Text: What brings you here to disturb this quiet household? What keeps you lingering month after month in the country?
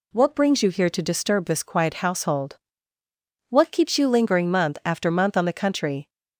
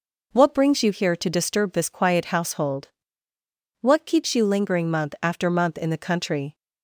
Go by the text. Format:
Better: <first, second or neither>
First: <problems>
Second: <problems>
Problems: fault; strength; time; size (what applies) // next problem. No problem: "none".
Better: second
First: says "on" for "in"; at 5.3 s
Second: none